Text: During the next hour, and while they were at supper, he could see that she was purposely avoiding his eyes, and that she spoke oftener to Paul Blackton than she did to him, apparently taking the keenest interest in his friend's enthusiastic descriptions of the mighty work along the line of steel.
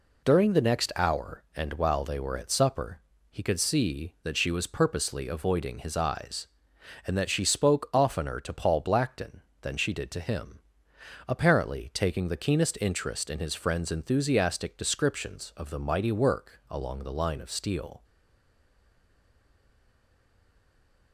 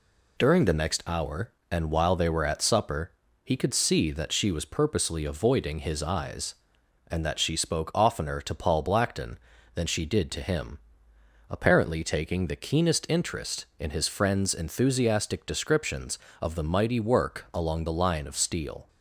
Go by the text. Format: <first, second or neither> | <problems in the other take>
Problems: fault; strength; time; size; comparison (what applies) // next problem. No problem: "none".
second | stays silent after the last word; strong; from 18.0 s on; 3.1 s long